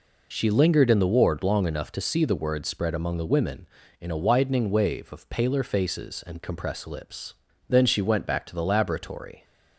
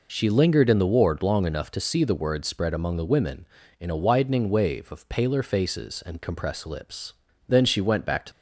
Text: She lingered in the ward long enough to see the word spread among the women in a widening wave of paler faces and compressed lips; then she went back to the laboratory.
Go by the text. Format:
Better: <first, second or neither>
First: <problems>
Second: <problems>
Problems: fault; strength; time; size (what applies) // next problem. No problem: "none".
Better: first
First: none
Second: stops before "the laboratory"; at 8.3 s